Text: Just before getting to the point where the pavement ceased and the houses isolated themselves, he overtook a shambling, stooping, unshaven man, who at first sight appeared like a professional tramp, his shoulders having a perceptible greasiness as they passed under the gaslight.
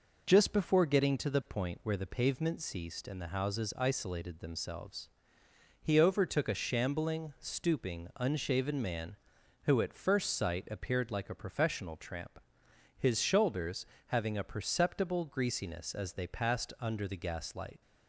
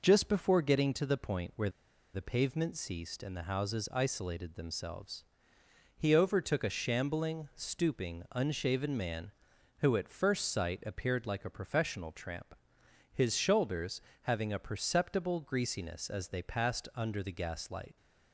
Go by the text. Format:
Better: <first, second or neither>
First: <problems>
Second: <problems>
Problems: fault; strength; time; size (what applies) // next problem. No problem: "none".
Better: first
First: pauses between "shoulders" and "having"; slight; at 13.8 s; 0.22 s long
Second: pauses between "where" and "the"; at 1.6 s; 0.44 s long // pauses between "shoulders" and "having"; slight; at 14.0 s; 0.22 s long